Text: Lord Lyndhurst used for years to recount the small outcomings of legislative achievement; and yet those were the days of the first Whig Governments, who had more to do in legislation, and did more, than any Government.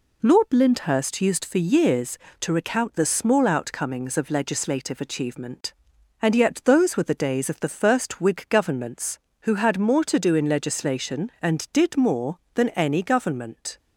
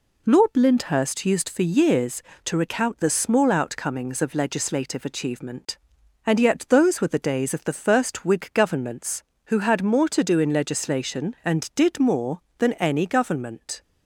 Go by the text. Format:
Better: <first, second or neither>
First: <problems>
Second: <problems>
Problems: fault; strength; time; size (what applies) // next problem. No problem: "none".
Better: neither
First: none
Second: none